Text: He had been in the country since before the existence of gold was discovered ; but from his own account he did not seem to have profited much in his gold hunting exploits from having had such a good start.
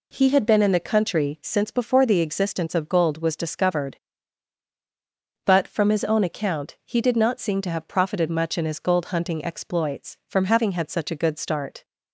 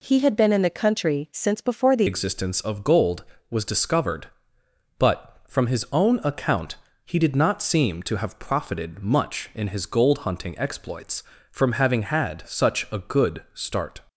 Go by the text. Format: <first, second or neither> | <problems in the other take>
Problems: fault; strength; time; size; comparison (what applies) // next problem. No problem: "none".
first | changes voice at "existence"; from 2.0 s on; 12.0 s long // pauses between "account" and "he"; slight; at 6.7 s; 0.30 s long